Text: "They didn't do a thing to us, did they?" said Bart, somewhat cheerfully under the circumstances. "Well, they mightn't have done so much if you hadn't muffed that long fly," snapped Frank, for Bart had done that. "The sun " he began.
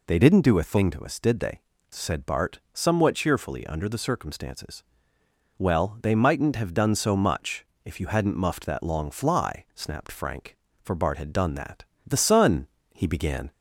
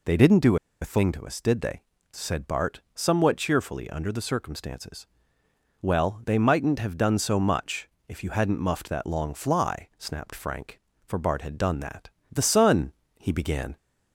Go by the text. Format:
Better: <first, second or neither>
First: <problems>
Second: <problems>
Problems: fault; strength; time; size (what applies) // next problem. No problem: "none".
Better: first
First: pauses between "much" and "if"; slight; at 7.6 s; 0.18 s long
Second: pauses between "do" and "a"; slight; at 0.5 s; 0.24 s long // pauses between "much" and "if"; slight; at 7.9 s; 0.18 s long